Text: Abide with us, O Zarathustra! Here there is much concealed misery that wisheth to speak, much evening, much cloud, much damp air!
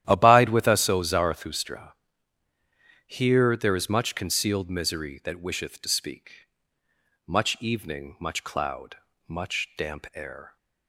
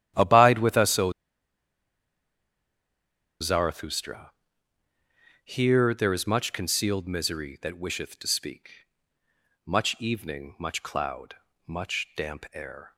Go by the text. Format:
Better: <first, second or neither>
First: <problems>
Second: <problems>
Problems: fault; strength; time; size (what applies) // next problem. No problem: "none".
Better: first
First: starts louder than the rest; strong; until 1.1 s; 11.5 dB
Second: starts louder than the rest; strong; until 3.4 s; 11.5 dB // pauses between "O" and "Zarathustra"; strong; at 1.1 s; 2.3 s long